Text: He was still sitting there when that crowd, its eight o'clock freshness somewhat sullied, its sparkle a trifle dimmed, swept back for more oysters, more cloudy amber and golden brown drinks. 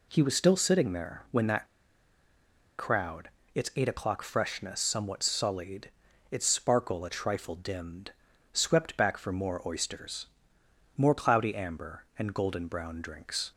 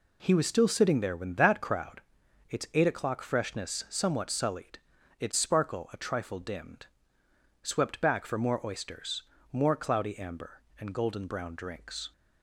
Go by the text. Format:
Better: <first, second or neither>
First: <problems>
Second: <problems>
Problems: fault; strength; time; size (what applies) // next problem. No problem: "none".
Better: second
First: pauses between "that" and "crowd"; at 1.6 s; 1.1 s long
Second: none